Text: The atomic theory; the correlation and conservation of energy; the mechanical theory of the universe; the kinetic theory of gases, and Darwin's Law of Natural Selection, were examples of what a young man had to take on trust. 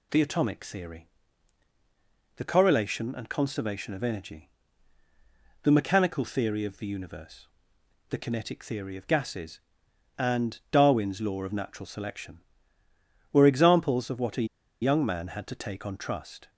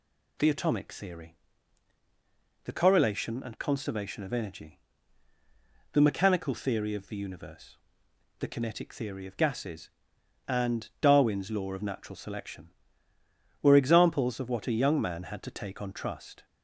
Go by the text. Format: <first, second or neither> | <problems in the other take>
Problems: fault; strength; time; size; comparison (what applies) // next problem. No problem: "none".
second | pauses between "a" and "young"; slight; at 14.4 s; 0.36 s long